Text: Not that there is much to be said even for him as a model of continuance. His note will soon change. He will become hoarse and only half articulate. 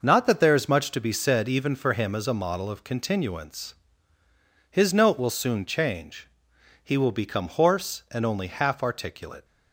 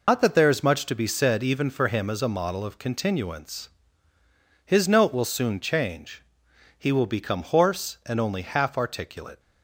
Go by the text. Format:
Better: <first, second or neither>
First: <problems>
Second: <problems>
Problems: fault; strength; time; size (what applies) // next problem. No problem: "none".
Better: first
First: none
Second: loses the start of "Not"; at 0.0 s; 105 ms